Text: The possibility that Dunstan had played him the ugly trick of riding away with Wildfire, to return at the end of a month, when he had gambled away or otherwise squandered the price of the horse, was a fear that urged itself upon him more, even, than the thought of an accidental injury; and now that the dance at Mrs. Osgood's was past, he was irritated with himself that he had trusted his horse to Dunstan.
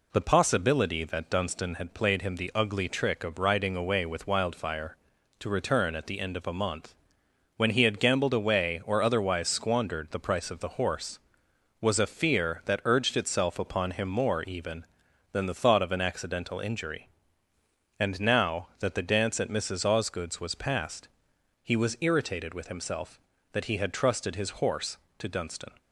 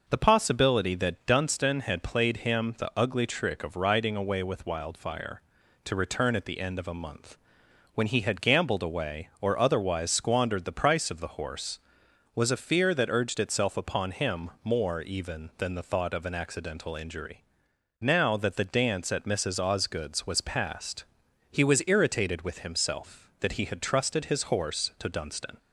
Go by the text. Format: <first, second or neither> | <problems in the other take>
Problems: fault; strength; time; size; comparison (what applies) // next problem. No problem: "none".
first | skips "and"; at 17.7 s